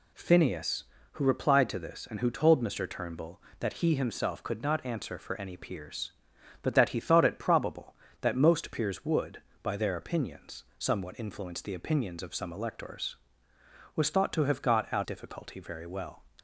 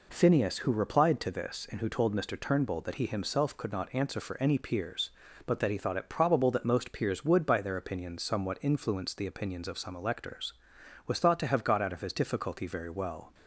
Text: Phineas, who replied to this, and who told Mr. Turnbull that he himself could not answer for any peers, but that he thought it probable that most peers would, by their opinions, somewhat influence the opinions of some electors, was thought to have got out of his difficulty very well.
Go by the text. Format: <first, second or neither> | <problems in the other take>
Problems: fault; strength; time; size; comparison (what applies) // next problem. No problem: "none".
second | skips "of his"; at 15.0 s